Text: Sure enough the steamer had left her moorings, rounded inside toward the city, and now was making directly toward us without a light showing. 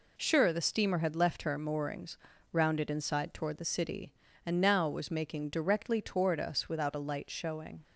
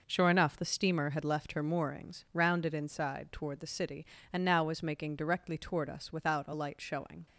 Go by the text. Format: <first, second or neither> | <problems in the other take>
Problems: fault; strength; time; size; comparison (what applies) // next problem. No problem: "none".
second | skips "enough"; at 0.5 s